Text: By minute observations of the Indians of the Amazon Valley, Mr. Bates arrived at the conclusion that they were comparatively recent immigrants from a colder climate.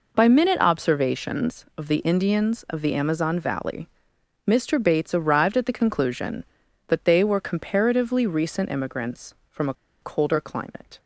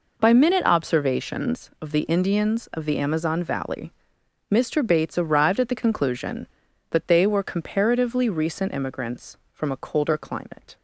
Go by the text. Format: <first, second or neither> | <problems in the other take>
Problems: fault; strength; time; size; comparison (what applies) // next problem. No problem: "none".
second | pauses between "a" and "colder"; slight; at 9.7 s; 0.27 s long